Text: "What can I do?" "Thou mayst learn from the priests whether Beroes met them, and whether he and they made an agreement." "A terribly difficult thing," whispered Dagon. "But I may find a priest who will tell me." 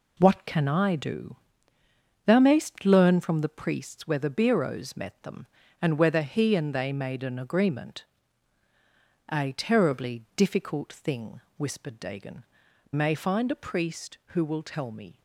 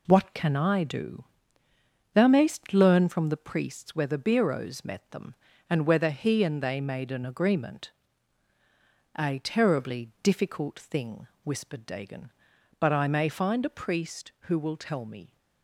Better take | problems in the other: second | skips "But I"; at 12.6 s

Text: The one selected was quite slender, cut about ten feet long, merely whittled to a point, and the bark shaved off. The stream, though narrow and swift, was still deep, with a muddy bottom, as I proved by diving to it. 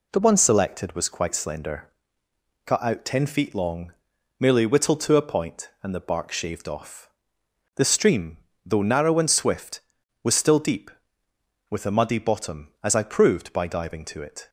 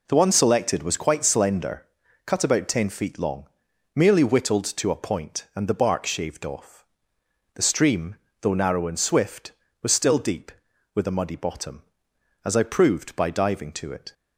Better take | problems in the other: second | says "out" for "about"; at 2.8 s

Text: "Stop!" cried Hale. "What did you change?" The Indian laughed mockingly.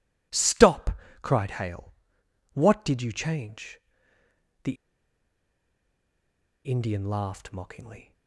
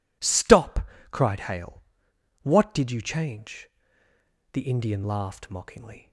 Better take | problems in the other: second | pauses between "The" and "Indian"; strong; at 4.7 s; 1.9 s long

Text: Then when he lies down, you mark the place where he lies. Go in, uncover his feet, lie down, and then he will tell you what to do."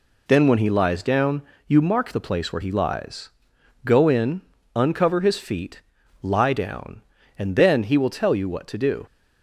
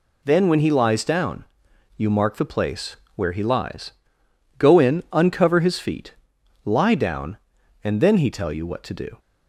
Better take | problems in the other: first | pauses between "place" and "where"; slight; at 2.9 s; 0.20 s long // skips "will"; at 8.2 s

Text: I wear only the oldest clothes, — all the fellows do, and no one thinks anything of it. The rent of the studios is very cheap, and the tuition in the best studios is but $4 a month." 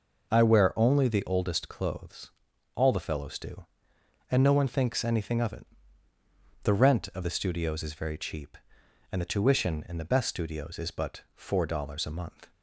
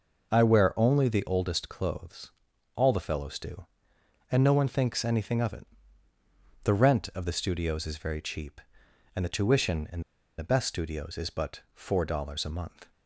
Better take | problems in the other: first | pauses between "in" and "the"; at 9.9 s; 0.38 s long

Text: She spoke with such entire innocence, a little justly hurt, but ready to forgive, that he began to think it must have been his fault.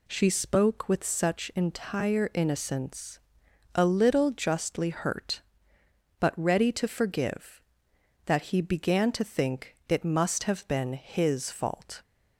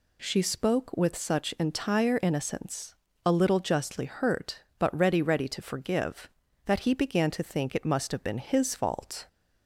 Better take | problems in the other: first | says "ready" twice; at 5.2 s

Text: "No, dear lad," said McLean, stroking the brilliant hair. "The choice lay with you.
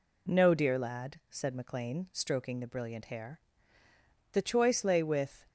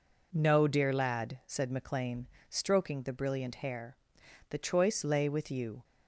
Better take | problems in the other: second | stops before "you"; at 5.4 s

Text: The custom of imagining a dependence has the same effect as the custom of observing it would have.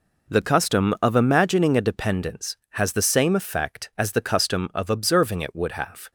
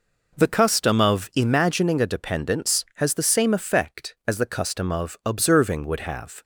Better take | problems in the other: first | skips "it"; at 5.8 s

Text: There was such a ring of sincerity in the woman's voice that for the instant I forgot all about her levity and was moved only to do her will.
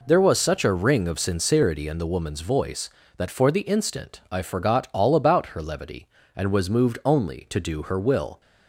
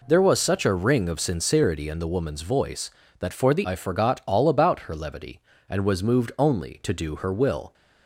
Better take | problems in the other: first | skips "instant"; at 3.6 s

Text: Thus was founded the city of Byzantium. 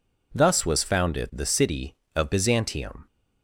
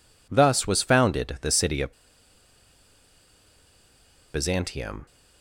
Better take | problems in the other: first | pauses between "of" and "Byzantium"; strong; at 1.9 s; 2.4 s long

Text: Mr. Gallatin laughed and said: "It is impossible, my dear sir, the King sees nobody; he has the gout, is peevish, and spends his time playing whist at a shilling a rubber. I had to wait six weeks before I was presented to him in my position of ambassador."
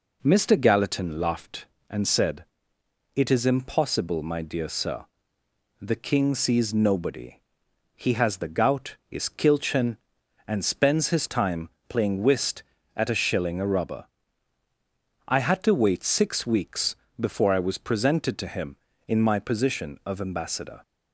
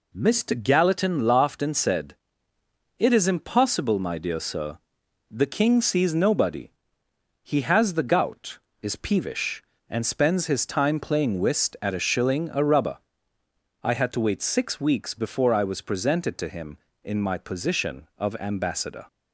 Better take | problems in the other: second | says "kilchen" for "peevish"; at 9.2 s // pauses between "time" and "playing"; slight; at 11.6 s; 0.18 s long // pauses between "weeks" and "before"; slight; at 16.9 s; 0.22 s long

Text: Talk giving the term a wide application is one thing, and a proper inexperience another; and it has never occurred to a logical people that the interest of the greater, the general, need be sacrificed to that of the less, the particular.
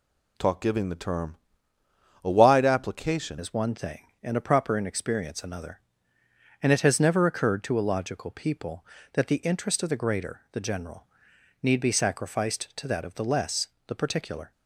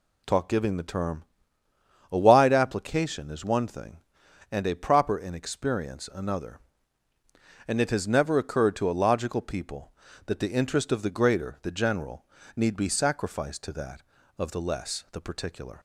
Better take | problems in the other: second | pauses between "term" and "a"; noticeable; at 1.3 s; 0.88 s long; noticeable in the second // changes voice at "is"; from 3.3 s on; 11.2 s long

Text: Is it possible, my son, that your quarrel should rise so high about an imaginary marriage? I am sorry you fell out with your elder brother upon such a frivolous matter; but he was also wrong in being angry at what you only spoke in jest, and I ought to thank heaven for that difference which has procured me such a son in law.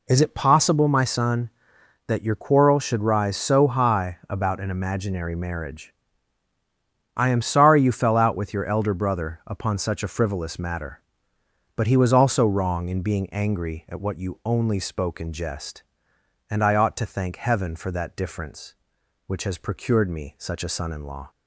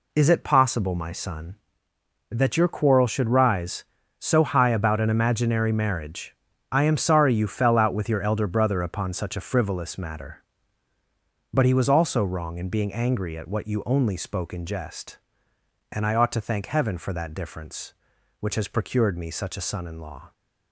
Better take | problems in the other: neither | none

